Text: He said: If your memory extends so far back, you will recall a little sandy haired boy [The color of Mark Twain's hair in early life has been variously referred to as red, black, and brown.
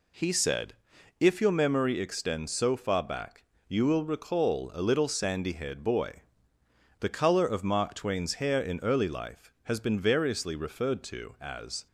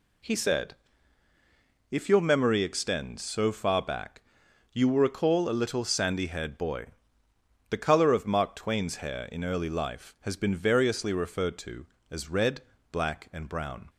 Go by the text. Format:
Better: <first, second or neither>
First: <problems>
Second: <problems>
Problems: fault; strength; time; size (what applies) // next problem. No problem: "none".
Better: second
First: pauses between "boy" and "The"; noticeable; at 6.2 s; 0.80 s long // stops before "red black and brown"; at 11.8 s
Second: pauses between "boy" and "The"; noticeable; at 6.8 s; 0.82 s long